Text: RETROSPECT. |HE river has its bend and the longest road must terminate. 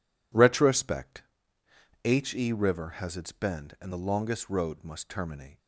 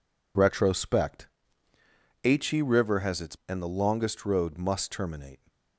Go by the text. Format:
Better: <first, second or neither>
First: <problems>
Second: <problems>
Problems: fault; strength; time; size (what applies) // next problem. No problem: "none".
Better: first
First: none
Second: skips "bend"; at 3.4 s